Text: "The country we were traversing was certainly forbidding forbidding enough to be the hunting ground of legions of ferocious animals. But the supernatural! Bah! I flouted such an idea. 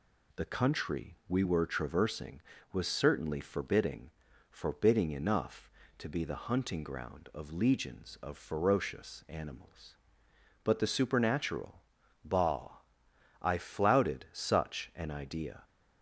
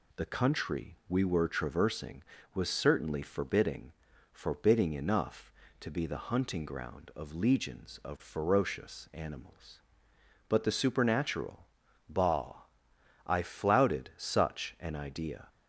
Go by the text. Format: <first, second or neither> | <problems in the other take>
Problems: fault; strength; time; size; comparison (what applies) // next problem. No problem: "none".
neither | pauses between "forbidding" and "forbidding"; the same in both